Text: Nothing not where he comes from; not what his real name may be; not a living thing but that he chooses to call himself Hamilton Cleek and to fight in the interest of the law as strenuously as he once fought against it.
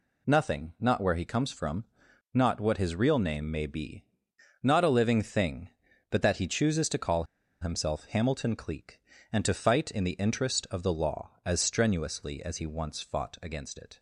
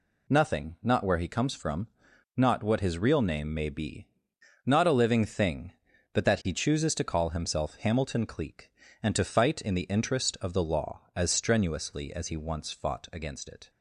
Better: second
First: pauses between "call" and "himself"; at 7.2 s; 0.37 s long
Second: none

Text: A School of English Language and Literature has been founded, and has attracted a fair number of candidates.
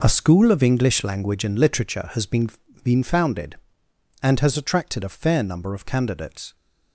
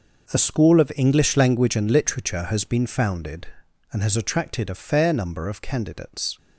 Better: second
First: says "been" twice; at 2.8 s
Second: none

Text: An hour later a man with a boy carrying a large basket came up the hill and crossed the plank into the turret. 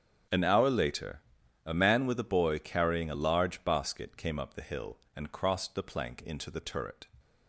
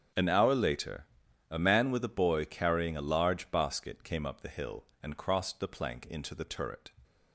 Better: neither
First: starts louder than the rest; strong; until 1.7 s; 7.5 dB // pauses between "later" and "a"; at 1.2 s; 0.42 s long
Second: starts louder than the rest; strong; until 1.5 s; 7.5 dB // pauses between "later" and "a"; at 1.0 s; 0.42 s long

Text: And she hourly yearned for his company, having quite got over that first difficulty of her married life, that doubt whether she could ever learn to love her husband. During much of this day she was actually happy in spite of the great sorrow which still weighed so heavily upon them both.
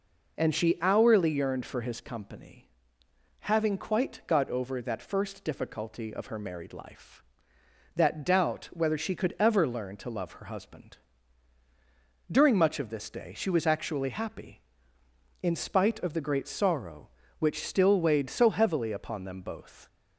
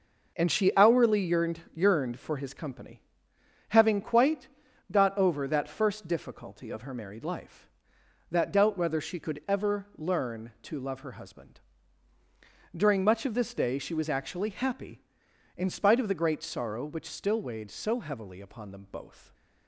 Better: first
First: none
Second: says "yearned" twice; at 1.7 s // pauses between "quite" and "got"; at 4.4 s; 0.44 s long

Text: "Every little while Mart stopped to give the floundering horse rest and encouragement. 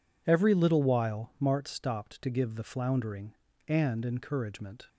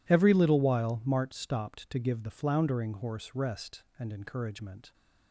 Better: second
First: skips "horse rest"; at 3.5 s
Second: none

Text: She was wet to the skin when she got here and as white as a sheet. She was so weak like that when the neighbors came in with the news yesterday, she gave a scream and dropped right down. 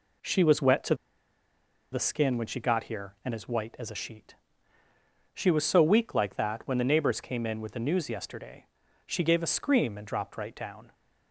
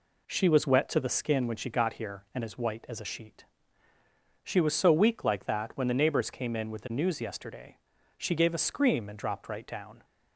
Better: second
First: pauses between "to" and "the"; at 0.9 s; 0.98 s long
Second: none

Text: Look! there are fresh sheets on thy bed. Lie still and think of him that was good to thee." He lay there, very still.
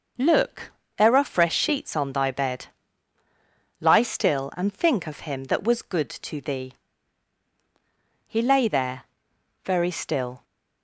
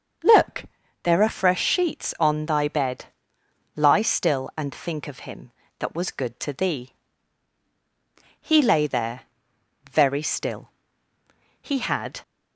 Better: first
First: none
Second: starts louder than the rest; until 1.6 s; 7 dB // goes on to say "He had"; from 11.6 s on; 0.60 s long

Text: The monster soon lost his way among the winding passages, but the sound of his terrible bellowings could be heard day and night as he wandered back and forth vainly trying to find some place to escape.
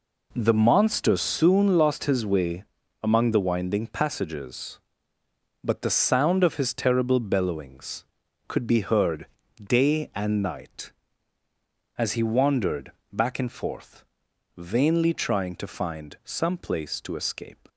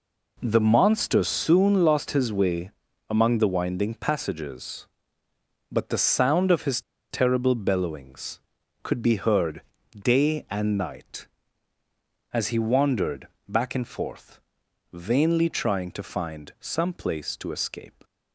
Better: first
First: pauses between "way" and "among"; at 2.6 s; 0.40 s long // pauses between "heard" and "day"; slight; at 9.2 s; 0.34 s long // pauses between "wandered" and "back"; slight; at 12.9 s; 0.20 s long // pauses between "forth" and "vainly"; noticeable; at 14.0 s; 0.52 s long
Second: pauses between "way" and "among"; at 2.7 s; 0.40 s long // pauses between "his" and "terrible"; slight; at 6.8 s; 0.30 s long // pauses between "heard" and "day"; slight; at 9.6 s; 0.34 s long // pauses between "wandered" and "back"; slight; at 13.2 s; 0.20 s long // pauses between "forth" and "vainly"; noticeable; at 14.3 s; 0.52 s long

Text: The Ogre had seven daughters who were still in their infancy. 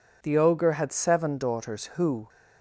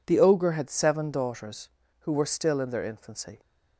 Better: second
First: stops before "were still in their infancy"; at 2.2 s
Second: none

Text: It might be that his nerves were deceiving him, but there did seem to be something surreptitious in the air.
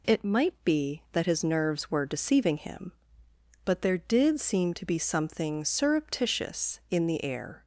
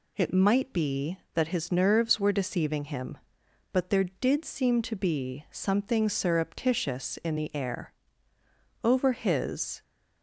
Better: first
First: none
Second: goes on to say "Over his"; noticeable; from 8.8 s on; 1.0 s long

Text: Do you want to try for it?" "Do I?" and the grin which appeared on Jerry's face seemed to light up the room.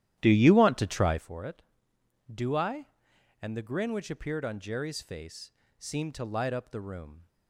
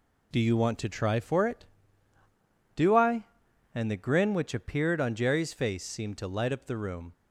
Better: second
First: starts louder than the rest; strong; until 1.3 s; 12.5 dB // pauses between "face" and "seemed"; slight; at 5.5 s; 0.26 s long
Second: none

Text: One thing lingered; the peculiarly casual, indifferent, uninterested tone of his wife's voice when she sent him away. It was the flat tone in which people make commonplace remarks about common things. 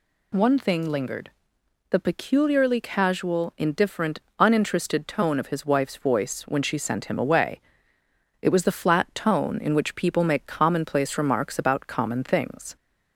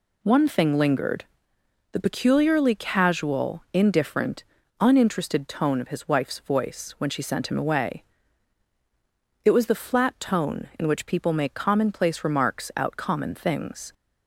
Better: first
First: none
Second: says "out" for "about"; at 12.7 s

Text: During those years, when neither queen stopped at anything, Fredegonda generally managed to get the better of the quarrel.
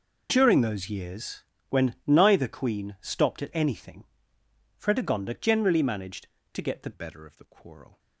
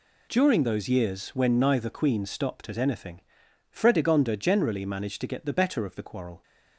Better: second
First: changes voice at "better"; from 6.9 s on; 1.0 s long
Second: none

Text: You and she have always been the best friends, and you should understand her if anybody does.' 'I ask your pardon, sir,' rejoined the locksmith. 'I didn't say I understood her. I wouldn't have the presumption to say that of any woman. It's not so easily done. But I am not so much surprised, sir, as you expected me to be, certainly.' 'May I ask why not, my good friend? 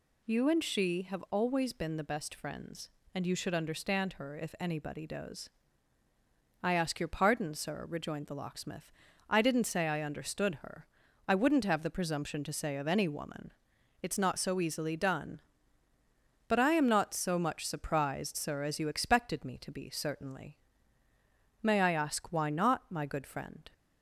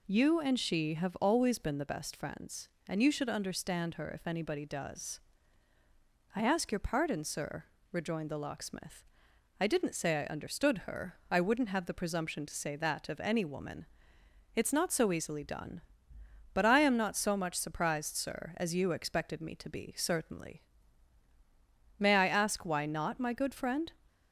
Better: second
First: skips "that"; at 12.7 s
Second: none

